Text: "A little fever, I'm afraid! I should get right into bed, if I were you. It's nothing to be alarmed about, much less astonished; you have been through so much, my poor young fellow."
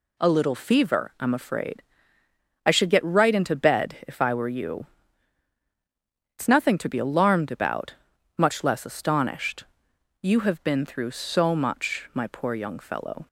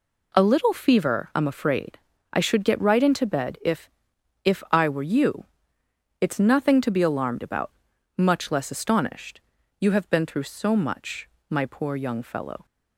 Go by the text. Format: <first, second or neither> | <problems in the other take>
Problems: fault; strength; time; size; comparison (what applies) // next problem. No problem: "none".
first | says "if" twice; at 4.4 s